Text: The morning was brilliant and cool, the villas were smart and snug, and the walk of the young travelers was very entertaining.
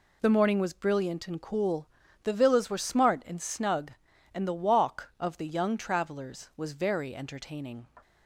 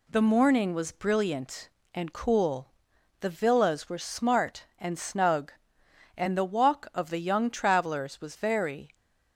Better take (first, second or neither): first